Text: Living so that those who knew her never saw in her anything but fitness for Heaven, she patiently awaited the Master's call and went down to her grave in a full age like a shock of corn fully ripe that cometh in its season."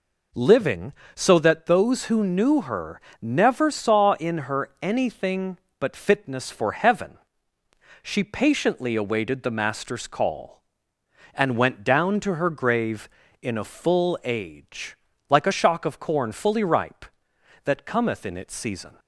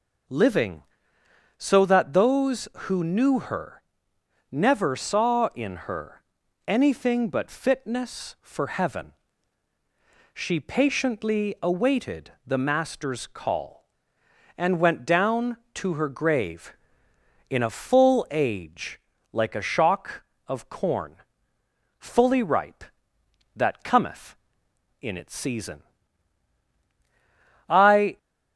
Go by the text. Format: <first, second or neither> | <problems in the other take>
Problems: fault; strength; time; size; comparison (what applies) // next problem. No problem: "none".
first | pauses between "her" and "never"; noticeable; at 3.8 s; 0.70 s long; slight in the first // pauses between "her" and "anything"; at 6.2 s; 0.44 s long // pauses between "age" and "like"; slight; at 18.9 s; 0.32 s long; slight in the first // pauses between "corn" and "fully"; noticeable; at 21.1 s; 0.82 s long // goes on to say "I"; from 27.6 s on; 0.50 s long